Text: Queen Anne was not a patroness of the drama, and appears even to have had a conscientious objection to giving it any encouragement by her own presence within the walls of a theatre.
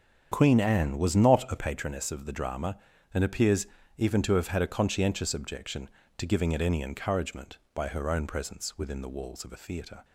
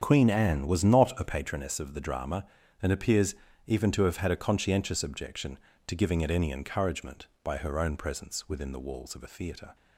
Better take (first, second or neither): neither